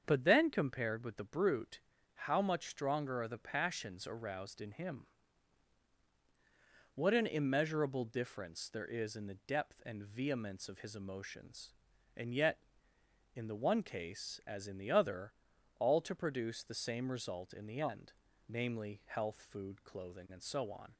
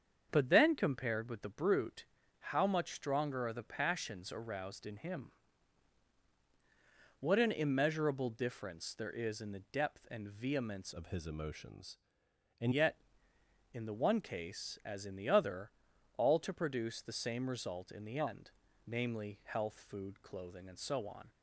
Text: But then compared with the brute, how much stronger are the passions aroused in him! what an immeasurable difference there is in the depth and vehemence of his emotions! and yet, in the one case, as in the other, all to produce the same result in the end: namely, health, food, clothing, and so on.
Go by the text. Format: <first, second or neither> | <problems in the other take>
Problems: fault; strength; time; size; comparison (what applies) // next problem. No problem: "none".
first | starts louder than the rest; strong; until 1.3 s; 7 dB; strong in the first // changes voice from "of" to "and"; from 10.9 to 12.7 s; 1.8 s long